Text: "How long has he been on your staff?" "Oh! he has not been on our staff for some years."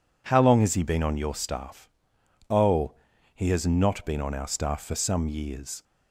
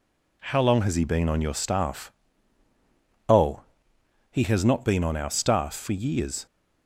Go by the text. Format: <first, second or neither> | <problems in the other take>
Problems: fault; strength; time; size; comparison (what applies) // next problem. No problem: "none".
first | skips "some"; at 5.9 s